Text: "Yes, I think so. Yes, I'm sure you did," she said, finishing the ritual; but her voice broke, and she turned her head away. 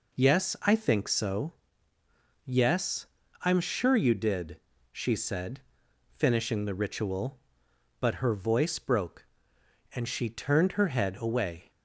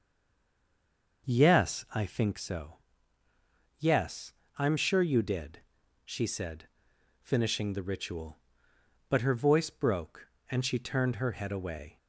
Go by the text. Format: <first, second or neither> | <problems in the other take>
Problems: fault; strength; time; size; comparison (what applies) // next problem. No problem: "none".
first | stays silent before the first word; noticeable; until 1.2 s; 1.2 s long